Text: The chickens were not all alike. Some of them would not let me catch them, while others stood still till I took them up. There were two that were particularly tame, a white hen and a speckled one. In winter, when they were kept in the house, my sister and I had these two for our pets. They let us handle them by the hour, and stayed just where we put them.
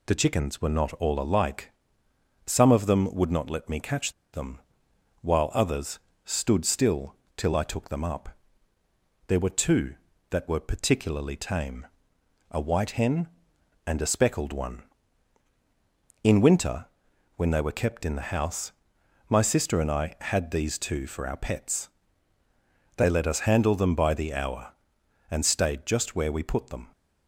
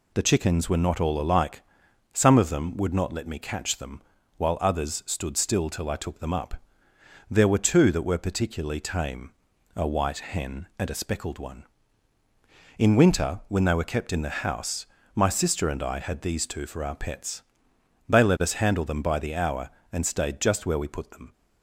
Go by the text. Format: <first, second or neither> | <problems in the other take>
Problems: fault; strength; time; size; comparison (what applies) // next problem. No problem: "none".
second | pauses between "catch" and "them"; slight; at 4.1 s; 0.20 s long // pauses between "others" and "stood"; slight; at 5.9 s; 0.26 s long // pauses between "still" and "till"; slight; at 7.1 s; 0.20 s long